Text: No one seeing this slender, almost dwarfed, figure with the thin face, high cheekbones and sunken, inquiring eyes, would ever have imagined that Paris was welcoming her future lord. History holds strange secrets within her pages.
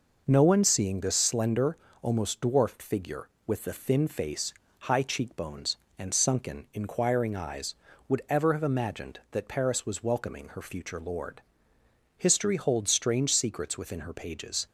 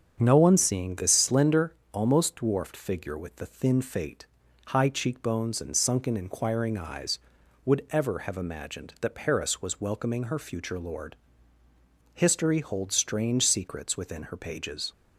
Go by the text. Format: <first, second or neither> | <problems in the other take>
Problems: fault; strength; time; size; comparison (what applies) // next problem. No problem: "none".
first | starts louder than the rest; strong; until 1.2 s; 7.5 dB // says "fate" for "face"; at 3.8 s